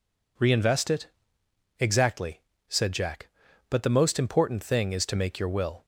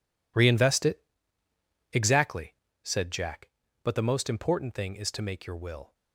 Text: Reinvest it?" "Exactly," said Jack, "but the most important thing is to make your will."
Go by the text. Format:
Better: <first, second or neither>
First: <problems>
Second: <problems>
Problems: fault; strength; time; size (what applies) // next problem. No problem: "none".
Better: first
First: none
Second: gets quieter; strong; throughout; 14 dB